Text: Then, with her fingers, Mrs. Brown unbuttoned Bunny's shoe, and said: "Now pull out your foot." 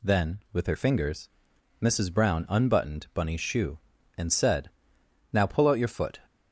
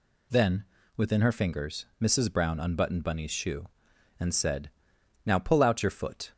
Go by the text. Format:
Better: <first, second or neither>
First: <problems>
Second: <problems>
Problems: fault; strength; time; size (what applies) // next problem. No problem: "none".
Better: first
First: none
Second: says "within" for "with"; at 0.9 s